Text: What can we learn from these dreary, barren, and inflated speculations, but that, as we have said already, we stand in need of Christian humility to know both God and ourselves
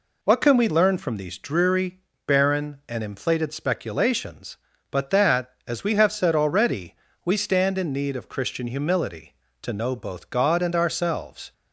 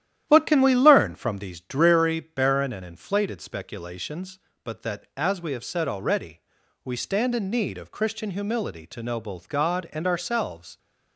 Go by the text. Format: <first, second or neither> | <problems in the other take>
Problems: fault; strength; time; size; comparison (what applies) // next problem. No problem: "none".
first | starts louder than the rest; strong; until 1.5 s; 11.5 dB